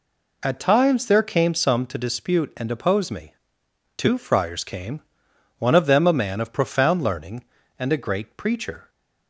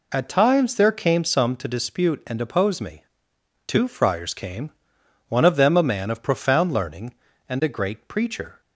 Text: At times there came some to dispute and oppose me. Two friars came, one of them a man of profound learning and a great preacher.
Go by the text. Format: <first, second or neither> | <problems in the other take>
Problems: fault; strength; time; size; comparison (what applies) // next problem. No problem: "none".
neither | none